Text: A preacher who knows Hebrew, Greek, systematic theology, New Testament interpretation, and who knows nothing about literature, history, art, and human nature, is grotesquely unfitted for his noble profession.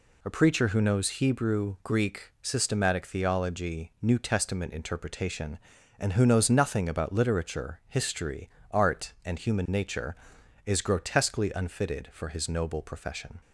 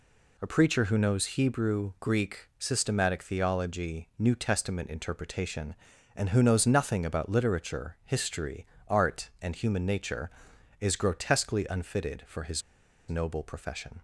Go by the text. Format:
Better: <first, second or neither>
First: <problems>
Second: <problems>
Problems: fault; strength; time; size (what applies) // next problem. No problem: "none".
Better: first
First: none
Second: pauses between "his" and "noble"; noticeable; at 12.6 s; 0.46 s long